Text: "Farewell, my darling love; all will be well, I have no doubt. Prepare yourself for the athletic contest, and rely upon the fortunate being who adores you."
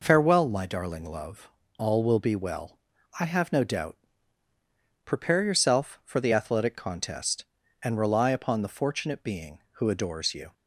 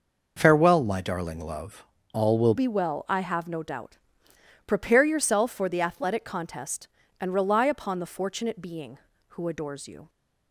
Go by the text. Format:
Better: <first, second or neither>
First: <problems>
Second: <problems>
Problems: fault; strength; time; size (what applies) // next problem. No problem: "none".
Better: first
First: none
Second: changes voice at "be"; from 2.5 s on; 7.5 s long